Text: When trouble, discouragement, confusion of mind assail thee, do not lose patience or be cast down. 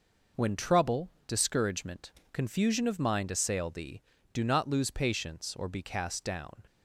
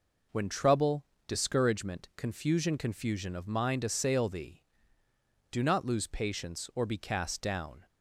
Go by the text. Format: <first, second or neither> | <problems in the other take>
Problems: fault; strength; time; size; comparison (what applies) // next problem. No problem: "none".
first | says "confusion" twice; at 2.7 s